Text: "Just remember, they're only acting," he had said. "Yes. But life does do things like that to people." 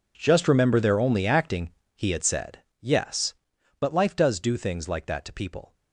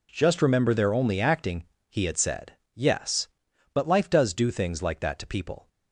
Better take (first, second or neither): second